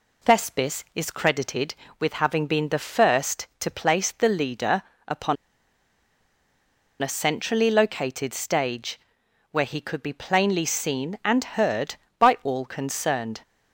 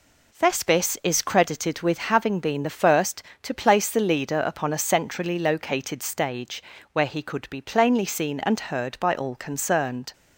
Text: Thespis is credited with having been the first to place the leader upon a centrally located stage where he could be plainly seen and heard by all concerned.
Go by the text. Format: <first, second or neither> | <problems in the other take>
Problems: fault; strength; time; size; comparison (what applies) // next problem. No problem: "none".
second | pauses between "leader" and "upon"; slight; at 4.8 s; 0.26 s long // pauses between "upon" and "a"; strong; at 5.3 s; 1.6 s long // pauses between "stage" and "where"; noticeable; at 8.9 s; 0.54 s long; slight in the second